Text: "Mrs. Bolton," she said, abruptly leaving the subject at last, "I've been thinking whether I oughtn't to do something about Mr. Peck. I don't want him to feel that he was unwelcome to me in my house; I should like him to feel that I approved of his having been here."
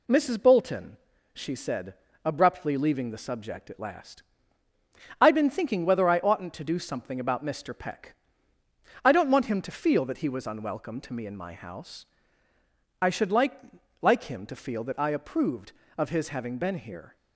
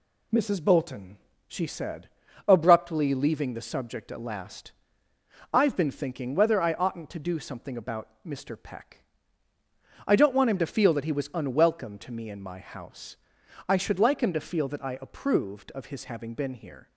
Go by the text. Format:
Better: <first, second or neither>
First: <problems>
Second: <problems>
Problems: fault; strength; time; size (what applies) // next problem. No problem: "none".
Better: second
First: says "like" twice; at 13.9 s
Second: none